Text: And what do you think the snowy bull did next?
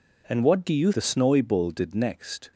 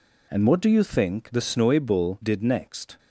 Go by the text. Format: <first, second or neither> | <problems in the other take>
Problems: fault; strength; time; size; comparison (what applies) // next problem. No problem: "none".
second | skips "think"; at 0.9 s